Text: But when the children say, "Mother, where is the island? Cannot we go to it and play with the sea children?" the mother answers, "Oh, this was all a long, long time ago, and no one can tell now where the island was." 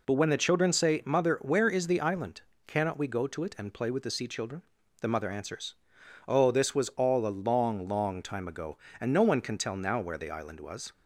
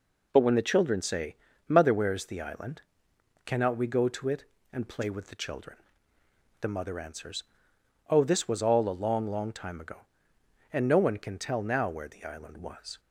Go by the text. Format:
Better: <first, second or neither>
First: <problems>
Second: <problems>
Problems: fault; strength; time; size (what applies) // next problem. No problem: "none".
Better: first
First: none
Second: skips "sea"; at 5.3 s